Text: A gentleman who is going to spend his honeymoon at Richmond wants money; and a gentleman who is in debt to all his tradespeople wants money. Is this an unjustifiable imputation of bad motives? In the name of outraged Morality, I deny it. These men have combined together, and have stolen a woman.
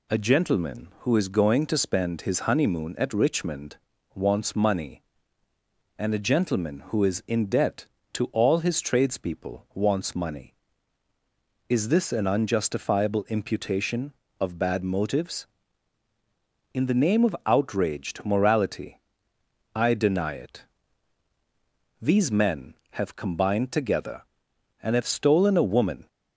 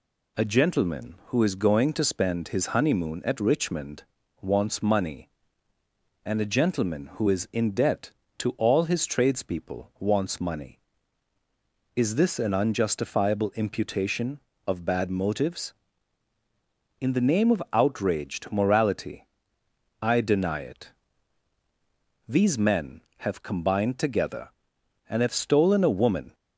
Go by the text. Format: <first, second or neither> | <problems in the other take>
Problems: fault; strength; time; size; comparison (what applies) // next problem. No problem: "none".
neither | pauses between "Richmond" and "wants"; slight; the same in both